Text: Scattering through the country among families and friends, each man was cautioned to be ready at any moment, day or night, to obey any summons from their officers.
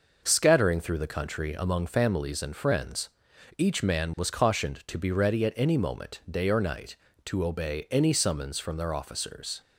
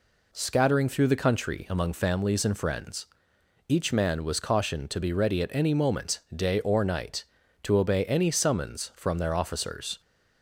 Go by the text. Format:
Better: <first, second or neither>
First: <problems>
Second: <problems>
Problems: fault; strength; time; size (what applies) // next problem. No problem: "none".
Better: neither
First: none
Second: none